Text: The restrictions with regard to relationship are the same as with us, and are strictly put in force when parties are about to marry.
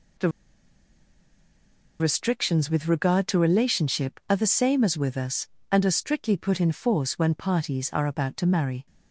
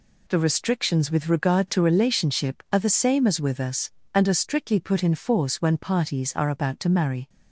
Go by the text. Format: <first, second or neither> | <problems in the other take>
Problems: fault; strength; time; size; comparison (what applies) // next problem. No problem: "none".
second | pauses between "The" and "restrictions"; strong; at 0.2 s; 1.7 s long